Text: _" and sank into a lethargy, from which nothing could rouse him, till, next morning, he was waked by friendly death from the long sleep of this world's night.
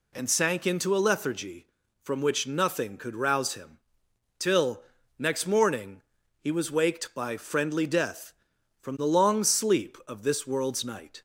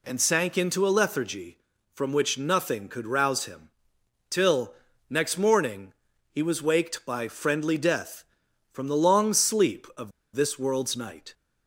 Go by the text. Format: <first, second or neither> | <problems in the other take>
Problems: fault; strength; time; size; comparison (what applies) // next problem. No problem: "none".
first | pauses between "of" and "this"; slight; at 10.1 s; 0.24 s long